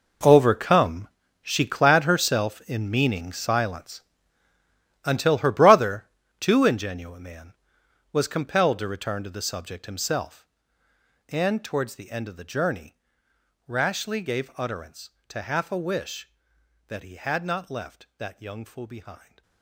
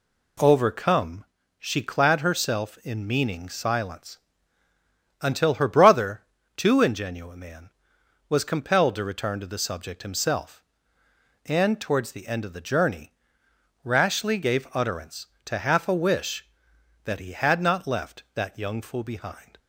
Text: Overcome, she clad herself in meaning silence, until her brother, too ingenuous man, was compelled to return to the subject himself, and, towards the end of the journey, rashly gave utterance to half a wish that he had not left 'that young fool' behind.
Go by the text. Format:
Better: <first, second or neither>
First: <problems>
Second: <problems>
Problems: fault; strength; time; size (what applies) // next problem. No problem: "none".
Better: second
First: gets quieter; strong; throughout; 15.5 dB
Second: none